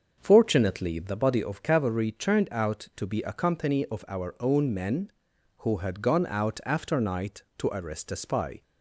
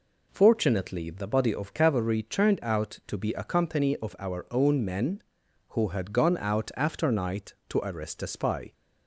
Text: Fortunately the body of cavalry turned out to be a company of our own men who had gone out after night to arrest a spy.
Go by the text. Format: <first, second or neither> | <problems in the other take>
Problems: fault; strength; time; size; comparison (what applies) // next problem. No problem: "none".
second | starts louder than the rest; until 1.4 s; 6.5 dB